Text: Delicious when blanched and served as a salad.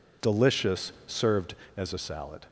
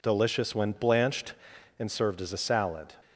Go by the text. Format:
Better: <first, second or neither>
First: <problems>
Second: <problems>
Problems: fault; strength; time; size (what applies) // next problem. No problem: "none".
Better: second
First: skips "when blanched and"; at 0.9 s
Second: none